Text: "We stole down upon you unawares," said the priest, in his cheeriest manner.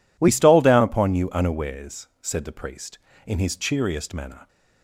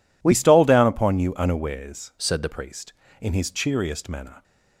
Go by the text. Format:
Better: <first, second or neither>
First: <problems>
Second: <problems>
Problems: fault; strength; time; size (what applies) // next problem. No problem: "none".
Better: first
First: none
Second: changes voice from "said" to "the"; from 2.1 to 2.4 s; 0.3 s long